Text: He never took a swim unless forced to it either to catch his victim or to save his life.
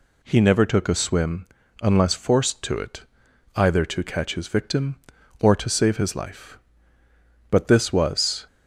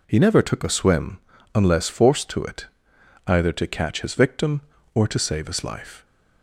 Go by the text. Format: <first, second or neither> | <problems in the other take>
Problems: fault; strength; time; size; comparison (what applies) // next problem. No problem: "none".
second | pauses between "swim" and "unless"; slight; at 1.4 s; 0.36 s long; slight in the second // pauses between "it" and "either"; noticeable; at 3.0 s; 0.54 s long; noticeable in the second // goes on to say "But this was"; noticeable; from 7.5 s on; 0.96 s long